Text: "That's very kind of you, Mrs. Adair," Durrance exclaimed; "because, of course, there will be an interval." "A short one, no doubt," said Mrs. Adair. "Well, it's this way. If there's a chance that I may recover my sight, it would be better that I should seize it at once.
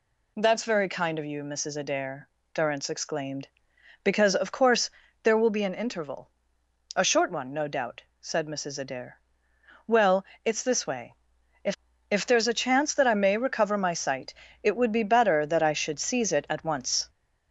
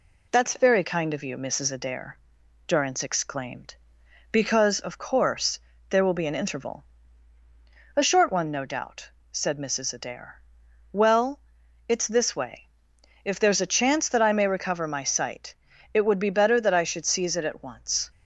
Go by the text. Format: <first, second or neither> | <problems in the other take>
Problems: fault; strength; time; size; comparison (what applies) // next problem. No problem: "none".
second | says "If" twice; at 12.0 s